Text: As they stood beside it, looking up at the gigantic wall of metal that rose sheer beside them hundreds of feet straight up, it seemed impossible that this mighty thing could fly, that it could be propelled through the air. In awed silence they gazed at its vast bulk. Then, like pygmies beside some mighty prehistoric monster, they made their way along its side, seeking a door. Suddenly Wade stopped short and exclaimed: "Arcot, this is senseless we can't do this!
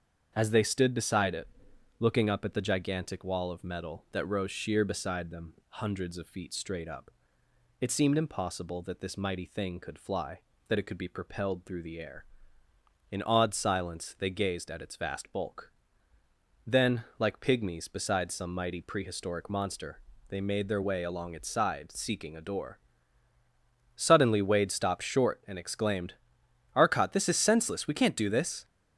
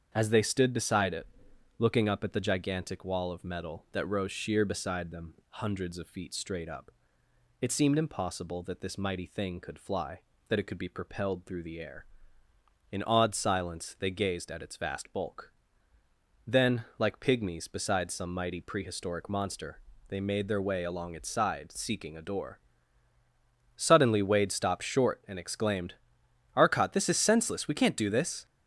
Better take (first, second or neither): neither